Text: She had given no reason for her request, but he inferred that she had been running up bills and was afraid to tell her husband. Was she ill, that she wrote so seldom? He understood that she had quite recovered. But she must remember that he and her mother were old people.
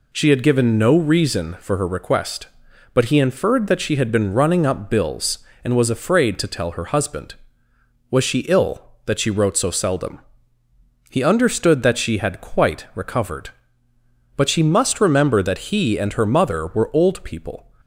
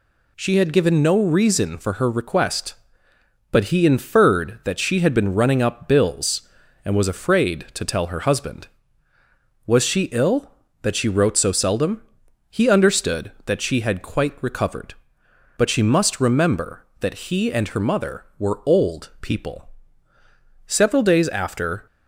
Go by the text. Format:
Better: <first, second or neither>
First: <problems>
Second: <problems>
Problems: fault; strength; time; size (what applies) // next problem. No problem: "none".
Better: first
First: none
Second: goes on to say "Several days after"; noticeable; from 20.6 s on; 1.2 s long